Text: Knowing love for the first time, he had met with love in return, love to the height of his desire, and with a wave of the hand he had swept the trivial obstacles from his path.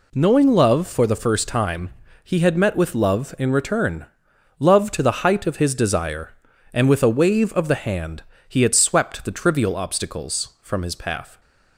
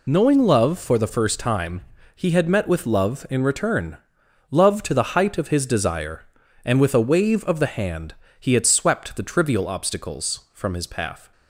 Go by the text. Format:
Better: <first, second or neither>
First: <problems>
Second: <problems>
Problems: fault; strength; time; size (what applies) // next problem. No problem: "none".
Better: first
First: pauses between "hand" and "he"; slight; at 8.2 s; 0.24 s long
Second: loses the start of "Knowing"; at 0.0 s; 35 ms // pauses between "hand" and "he"; slight; at 8.1 s; 0.24 s long